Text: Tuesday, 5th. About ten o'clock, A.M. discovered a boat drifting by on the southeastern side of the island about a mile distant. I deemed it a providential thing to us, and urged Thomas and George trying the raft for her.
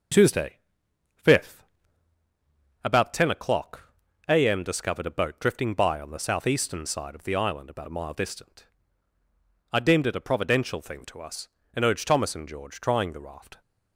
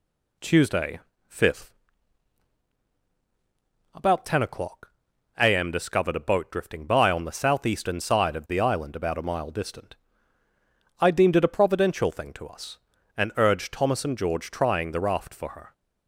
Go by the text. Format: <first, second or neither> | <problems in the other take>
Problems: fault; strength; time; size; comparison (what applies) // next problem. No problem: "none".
second | stops before "for her"; at 13.6 s